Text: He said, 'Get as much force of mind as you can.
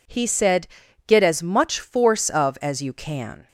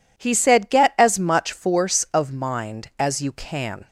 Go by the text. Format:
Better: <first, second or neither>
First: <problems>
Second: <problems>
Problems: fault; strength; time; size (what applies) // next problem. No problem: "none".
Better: second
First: skips "mind"; at 2.5 s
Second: none